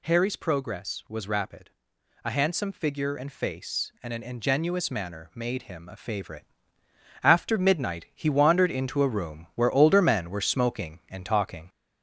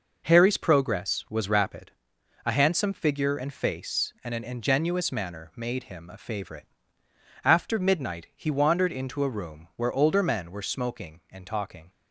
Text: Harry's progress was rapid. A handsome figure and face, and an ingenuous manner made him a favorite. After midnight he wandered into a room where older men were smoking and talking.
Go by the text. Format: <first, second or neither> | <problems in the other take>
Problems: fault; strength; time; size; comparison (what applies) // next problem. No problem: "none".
second | gets louder; slight; throughout; 3 dB